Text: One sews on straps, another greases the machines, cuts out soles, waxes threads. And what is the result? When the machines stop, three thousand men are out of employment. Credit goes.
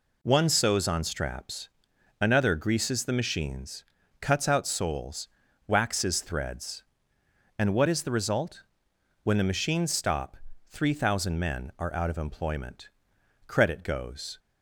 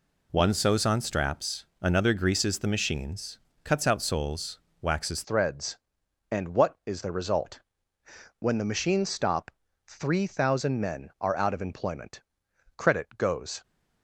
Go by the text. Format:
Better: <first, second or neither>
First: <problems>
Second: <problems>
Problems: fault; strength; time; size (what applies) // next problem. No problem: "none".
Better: first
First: none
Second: changes voice at "threads"; from 5.2 s on; 8.4 s long